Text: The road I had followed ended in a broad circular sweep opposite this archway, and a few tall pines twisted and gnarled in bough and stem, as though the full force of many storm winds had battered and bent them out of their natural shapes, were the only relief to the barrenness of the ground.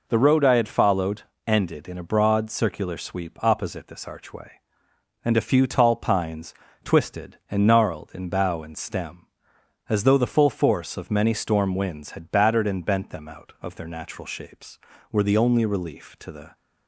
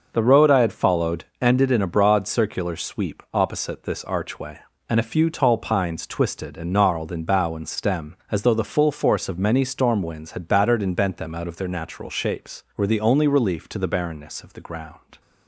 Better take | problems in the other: second | pauses between "followed" and "ended"; slight; at 1.2 s; 0.24 s long; slight in the second // pauses between "pines" and "twisted"; slight; at 6.5 s; 0.30 s long // stops before "barrenness of the ground"; at 16.5 s

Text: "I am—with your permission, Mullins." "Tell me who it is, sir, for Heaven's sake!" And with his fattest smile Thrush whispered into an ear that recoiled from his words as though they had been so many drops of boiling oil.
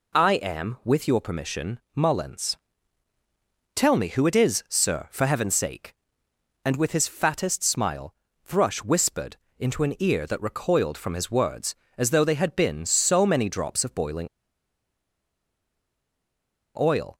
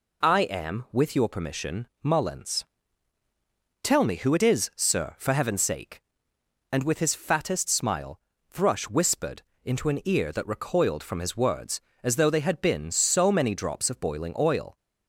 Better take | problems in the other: second | pauses between "smile" and "Thrush"; slight; at 8.1 s; 0.32 s long; slight in the second // pauses between "whispered" and "into"; slight; at 9.3 s; 0.22 s long; slight in the second // pauses between "boiling" and "oil"; strong; at 14.2 s; 2.4 s long

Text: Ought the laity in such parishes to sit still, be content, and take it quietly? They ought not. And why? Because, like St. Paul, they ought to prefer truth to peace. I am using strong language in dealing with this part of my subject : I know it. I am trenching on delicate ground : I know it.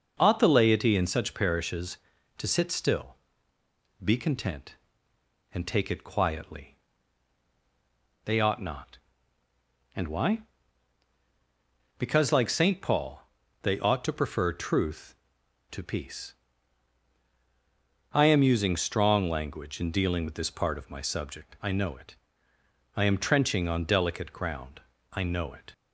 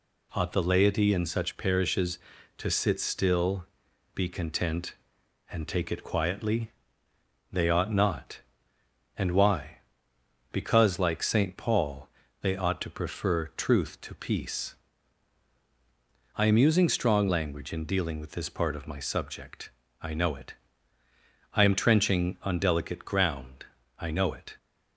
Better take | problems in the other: neither | none

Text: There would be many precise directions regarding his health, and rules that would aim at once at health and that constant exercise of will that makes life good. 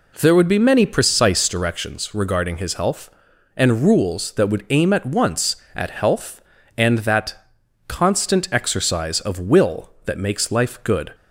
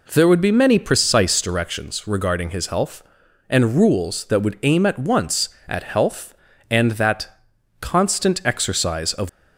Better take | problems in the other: first | pauses between "that" and "constant"; noticeable; at 7.2 s; 0.52 s long; noticeable in the first // stops before "will that makes life good"; at 9.2 s

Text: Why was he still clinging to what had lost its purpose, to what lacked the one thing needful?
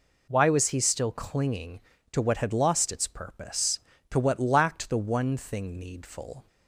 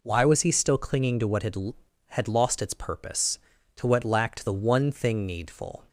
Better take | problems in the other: first | says "had" twice; at 2.0 s

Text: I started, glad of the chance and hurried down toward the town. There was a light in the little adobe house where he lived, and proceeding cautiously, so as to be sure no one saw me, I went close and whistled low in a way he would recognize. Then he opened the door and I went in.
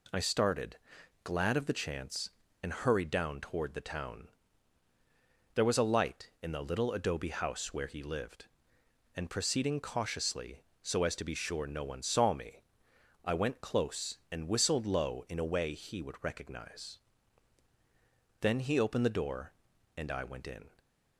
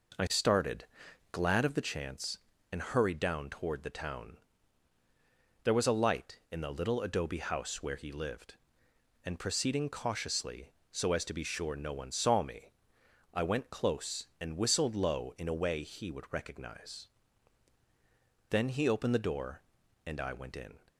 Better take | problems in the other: first | starts louder than the rest; noticeable; until 1.8 s; 5 dB

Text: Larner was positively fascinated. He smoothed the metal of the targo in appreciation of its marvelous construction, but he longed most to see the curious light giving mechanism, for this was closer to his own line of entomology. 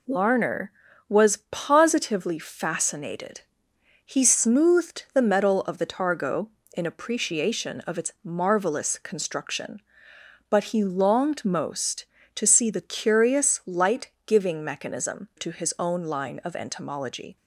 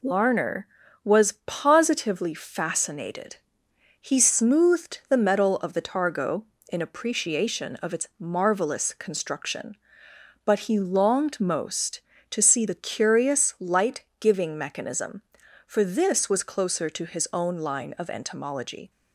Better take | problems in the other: second | pauses between "light" and "giving"; slight; at 14.1 s; 0.16 s long; slight in the second // skips "for this was closer"; at 15.3 s

